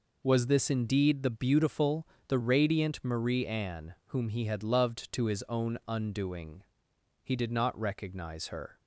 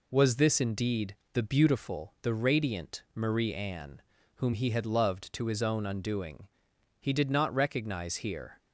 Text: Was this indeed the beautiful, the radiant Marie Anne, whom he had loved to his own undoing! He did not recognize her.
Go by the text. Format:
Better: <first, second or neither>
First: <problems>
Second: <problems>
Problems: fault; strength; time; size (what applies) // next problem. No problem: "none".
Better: first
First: none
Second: pauses between "indeed" and "the"; slight; at 1.1 s; 0.16 s long // says "here" for "her"; at 8.1 s